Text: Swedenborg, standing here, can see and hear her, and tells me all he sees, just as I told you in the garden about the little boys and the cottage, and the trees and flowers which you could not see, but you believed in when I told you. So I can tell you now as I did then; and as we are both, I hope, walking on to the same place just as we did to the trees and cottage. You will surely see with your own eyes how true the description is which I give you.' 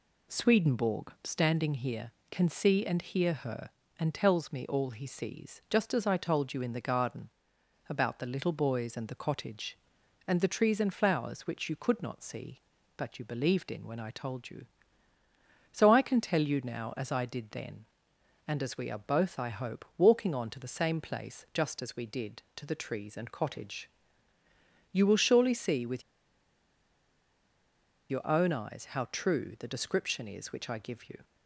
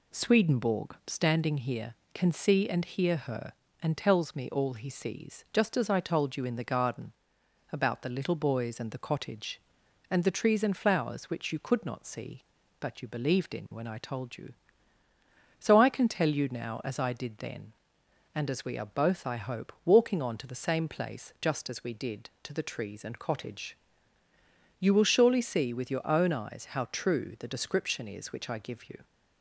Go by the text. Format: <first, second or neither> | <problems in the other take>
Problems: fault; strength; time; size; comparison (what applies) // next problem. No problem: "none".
second | pauses between "garden" and "about"; noticeable; at 7.3 s; 0.58 s long; noticeable in the second // pauses between "with" and "your"; strong; at 26.0 s; 2.0 s long